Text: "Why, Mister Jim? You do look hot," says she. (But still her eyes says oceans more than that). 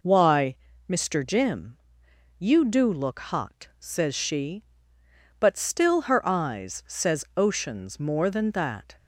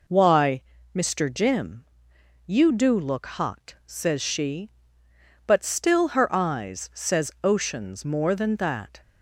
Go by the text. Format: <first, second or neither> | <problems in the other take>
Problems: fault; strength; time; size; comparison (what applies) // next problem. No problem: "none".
neither | none